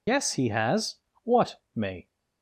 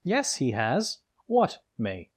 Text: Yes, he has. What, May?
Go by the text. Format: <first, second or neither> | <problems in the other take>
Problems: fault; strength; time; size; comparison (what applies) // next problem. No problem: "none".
second | loses the start of "Yes"; at 0.0 s; 55 ms